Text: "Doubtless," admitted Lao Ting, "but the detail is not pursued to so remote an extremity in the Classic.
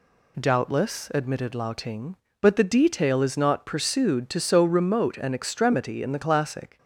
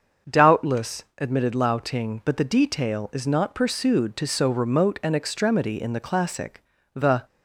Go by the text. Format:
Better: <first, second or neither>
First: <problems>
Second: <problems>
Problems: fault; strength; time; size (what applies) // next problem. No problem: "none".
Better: first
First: none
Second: starts louder than the rest; until 1.4 s; 6.5 dB // goes on to say "The"; slight; from 6.9 s on; 0.32 s long